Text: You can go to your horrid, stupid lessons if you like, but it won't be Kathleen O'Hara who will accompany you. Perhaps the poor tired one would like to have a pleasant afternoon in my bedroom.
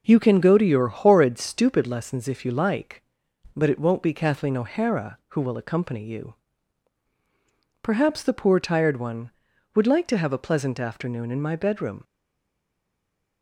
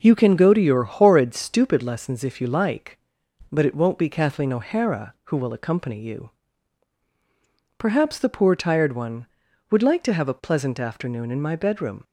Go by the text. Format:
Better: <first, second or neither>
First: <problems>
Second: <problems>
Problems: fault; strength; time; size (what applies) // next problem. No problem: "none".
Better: second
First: stays silent after the last word; noticeable; from 12.0 s on; 1.4 s long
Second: none